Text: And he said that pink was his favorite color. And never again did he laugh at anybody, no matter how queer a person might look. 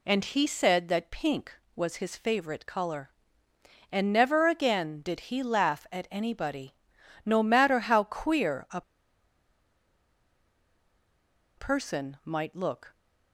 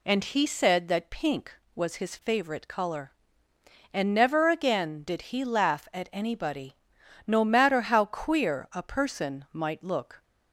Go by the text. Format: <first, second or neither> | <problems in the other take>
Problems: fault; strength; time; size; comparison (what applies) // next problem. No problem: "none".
second | pauses between "a" and "person"; strong; at 8.8 s; 2.7 s long